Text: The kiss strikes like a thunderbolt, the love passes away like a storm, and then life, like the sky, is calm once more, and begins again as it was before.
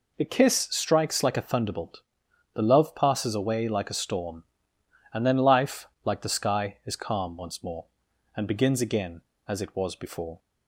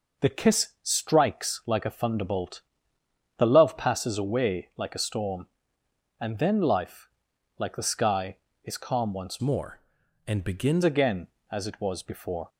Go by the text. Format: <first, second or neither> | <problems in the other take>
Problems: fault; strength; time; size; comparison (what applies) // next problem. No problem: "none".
first | changes voice from "more" to "begins"; from 9.4 to 10.8 s; 1.4 s long